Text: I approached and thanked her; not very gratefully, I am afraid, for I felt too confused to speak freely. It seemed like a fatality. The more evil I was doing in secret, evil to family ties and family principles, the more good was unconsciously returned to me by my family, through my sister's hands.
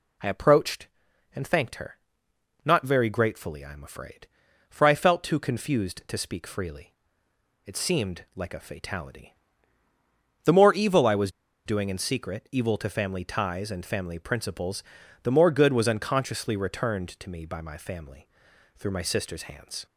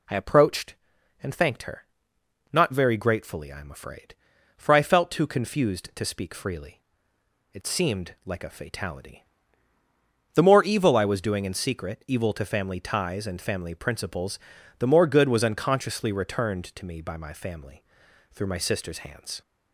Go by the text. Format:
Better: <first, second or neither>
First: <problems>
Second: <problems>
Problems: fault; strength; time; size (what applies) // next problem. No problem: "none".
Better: second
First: pauses between "was" and "doing"; at 11.2 s; 0.36 s long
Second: none